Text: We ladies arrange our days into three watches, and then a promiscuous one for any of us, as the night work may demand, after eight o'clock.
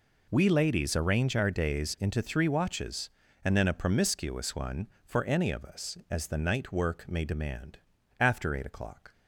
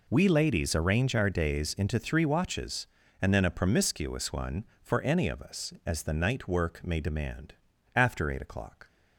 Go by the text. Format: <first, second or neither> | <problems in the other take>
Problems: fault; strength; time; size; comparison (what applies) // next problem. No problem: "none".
neither | none